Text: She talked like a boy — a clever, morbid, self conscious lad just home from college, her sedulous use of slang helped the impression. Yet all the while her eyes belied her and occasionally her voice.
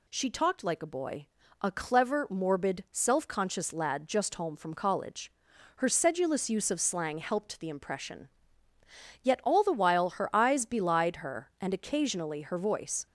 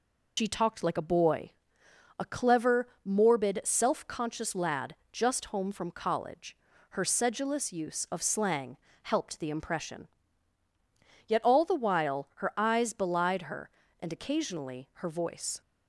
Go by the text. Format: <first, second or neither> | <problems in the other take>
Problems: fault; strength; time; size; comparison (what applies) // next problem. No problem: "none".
first | loses the start of "She"; at 0.3 s; 110 ms // pauses between "lad" and "just"; slight; at 4.9 s; 0.16 s long // pauses between "slang" and "helped"; slight; at 8.7 s; 0.26 s long